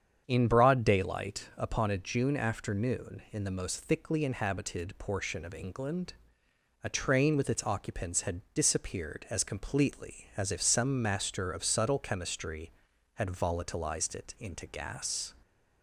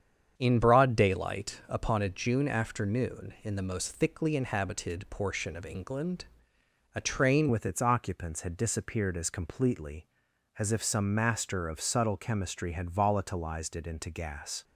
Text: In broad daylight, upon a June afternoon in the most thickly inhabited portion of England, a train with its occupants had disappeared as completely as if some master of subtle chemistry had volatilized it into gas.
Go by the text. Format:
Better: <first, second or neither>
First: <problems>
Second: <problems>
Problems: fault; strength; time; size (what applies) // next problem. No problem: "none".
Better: first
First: starts louder than the rest; strong; until 1.2 s; 8 dB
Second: starts louder than the rest; strong; until 1.3 s; 8 dB // changes voice at "with"; from 7.5 s on; 7.1 s long